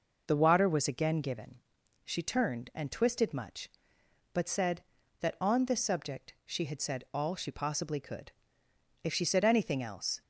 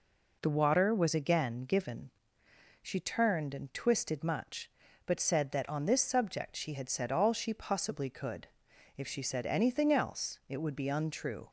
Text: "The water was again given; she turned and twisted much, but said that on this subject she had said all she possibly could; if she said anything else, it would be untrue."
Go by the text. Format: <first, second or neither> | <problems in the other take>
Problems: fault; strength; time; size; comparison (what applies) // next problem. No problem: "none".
second | stops before "it would be untrue"; at 10.2 s